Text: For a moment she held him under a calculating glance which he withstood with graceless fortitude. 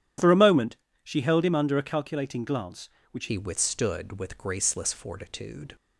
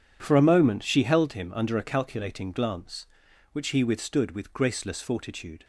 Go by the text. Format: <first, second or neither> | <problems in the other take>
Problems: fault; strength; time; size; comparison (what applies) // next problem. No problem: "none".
second | starts louder than the rest; strong; until 1.4 s; 11 dB // pauses between "moment" and "she"; slight; at 0.7 s; 0.30 s long // changes voice at "he"; from 3.2 s on; 2.5 s long